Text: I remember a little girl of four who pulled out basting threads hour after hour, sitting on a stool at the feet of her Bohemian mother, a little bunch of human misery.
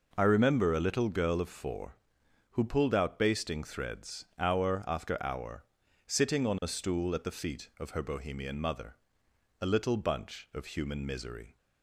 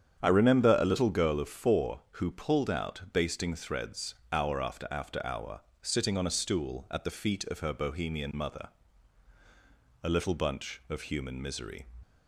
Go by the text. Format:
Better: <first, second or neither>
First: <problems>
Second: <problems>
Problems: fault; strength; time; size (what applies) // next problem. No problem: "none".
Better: first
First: none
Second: starts louder than the rest; strong; until 1.2 s; 8 dB // pauses between "threads" and "hour"; slight; at 4.1 s; 0.16 s long // says "after" twice; at 4.8 s